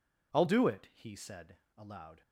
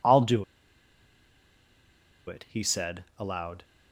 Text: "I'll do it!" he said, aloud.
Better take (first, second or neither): first